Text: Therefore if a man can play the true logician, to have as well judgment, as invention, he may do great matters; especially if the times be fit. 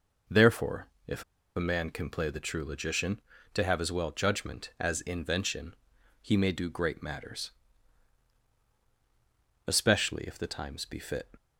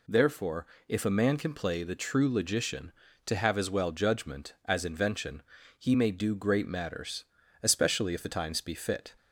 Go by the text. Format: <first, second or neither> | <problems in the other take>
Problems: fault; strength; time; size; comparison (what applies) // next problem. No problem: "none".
second | pauses between "Therefore" and "if"; slight; at 0.8 s; 0.20 s long; slight in the second // pauses between "if" and "a"; slight; at 1.2 s; 0.33 s long